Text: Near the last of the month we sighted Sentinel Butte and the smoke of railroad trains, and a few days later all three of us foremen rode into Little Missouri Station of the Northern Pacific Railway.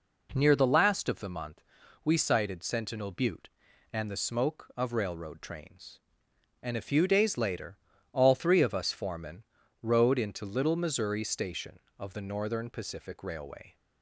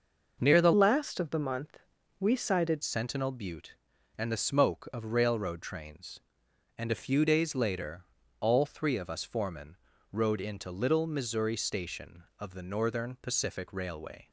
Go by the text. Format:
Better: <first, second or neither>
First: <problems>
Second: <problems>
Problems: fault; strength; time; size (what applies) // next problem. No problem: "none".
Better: first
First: pauses between "month" and "we"; at 1.6 s; 0.44 s long // pauses between "later" and "all"; slight; at 7.7 s; 0.36 s long // pauses between "foremen" and "rode"; at 9.4 s; 0.40 s long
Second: starts louder than the rest; noticeable; until 1.4 s; 6 dB // changes voice from "last" to "sighted"; from 0.7 to 2.8 s; 2.1 s long // pauses between "month" and "we"; at 1.7 s; 0.40 s long // pauses between "later" and "all"; slight; at 8.0 s; 0.34 s long // pauses between "foremen" and "rode"; slight; at 9.7 s; 0.34 s long